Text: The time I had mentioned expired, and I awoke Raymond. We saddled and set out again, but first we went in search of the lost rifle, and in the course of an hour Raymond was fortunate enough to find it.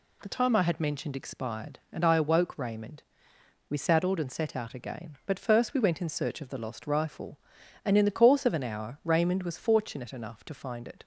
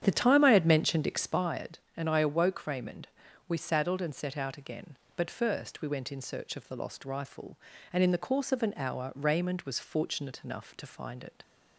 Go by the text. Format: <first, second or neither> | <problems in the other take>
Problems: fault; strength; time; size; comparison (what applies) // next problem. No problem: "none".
first | starts louder than the rest; strong; until 1.6 s; 9.5 dB